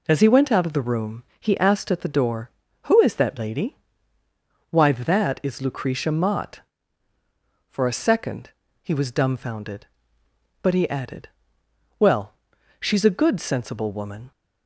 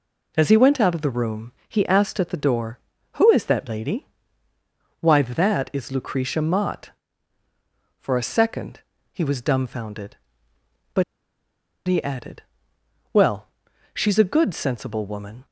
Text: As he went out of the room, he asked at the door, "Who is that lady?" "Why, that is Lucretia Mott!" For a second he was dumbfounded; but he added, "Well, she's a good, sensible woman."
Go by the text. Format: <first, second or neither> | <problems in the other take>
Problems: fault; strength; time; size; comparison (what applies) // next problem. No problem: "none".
first | pauses between "second" and "he"; slight; at 8.7 s; 0.34 s long; slight in the first // pauses between "but" and "he"; noticeable; at 11.0 s; 0.83 s long